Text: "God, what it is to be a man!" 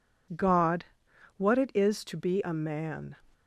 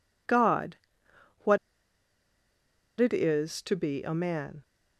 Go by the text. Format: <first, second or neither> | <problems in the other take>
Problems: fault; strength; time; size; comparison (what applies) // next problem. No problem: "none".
first | pauses between "what" and "it"; strong; at 1.5 s; 1.4 s long